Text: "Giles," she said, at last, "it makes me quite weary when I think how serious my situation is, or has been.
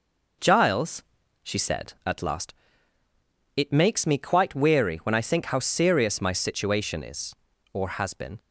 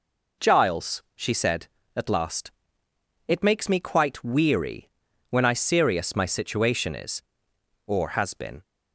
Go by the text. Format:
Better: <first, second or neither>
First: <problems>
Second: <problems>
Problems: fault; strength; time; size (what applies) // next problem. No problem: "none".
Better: first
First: none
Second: pauses between "weary" and "when"; at 4.8 s; 0.42 s long // skips "think how"; at 5.5 s